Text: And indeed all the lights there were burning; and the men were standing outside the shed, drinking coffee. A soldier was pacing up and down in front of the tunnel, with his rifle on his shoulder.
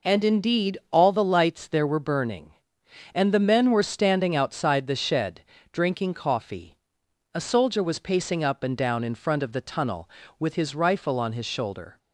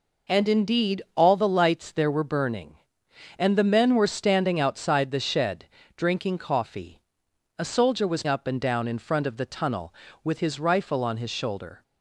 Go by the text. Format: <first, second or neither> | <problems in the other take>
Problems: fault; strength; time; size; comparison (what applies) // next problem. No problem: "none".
first | skips "pacing"; at 8.2 s